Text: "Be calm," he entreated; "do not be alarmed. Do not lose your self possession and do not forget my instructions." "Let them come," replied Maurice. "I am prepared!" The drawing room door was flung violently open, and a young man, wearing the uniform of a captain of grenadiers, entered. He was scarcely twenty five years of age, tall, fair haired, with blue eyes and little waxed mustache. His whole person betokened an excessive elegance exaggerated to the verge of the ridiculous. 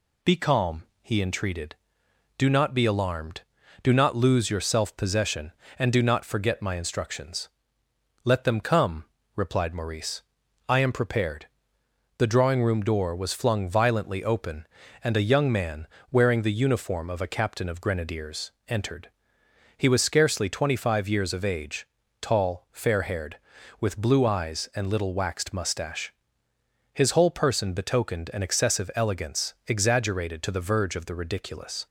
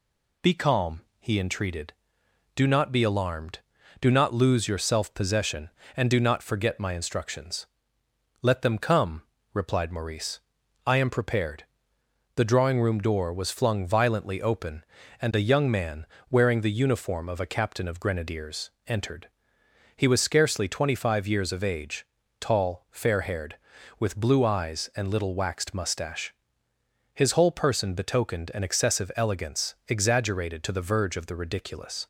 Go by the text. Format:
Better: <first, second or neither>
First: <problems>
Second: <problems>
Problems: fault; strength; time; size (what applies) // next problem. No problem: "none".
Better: neither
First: none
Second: none